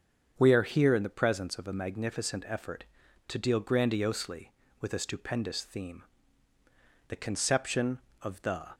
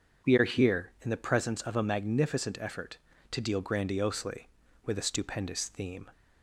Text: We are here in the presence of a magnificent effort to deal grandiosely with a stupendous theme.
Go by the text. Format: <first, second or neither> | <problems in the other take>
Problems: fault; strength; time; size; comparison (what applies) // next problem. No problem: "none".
second | starts louder than the rest; strong; until 1.3 s; 7.5 dB // goes on to say "The conception of the"; from 7.0 s on; 1.6 s long